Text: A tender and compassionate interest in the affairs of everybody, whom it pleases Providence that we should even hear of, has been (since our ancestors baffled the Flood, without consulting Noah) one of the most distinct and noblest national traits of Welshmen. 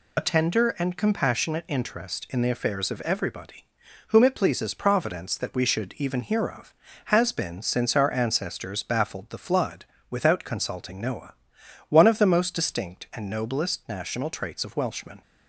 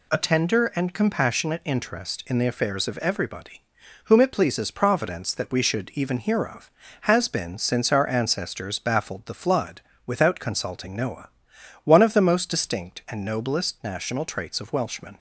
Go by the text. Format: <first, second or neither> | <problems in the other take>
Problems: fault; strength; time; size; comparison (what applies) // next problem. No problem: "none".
second | loses the start of "A"; at 0.1 s; 25 ms